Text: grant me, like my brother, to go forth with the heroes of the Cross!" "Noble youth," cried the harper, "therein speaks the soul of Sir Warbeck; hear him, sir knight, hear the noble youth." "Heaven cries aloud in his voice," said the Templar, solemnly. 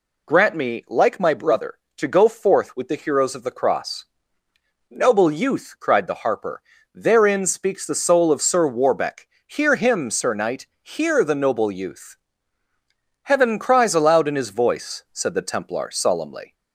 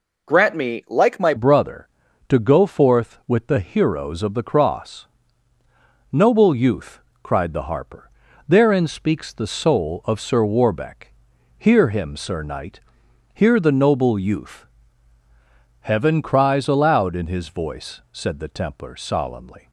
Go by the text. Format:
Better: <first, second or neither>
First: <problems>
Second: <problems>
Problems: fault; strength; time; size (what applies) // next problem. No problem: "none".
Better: first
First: none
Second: changes voice at "brother"; from 1.3 s on; 18.3 s long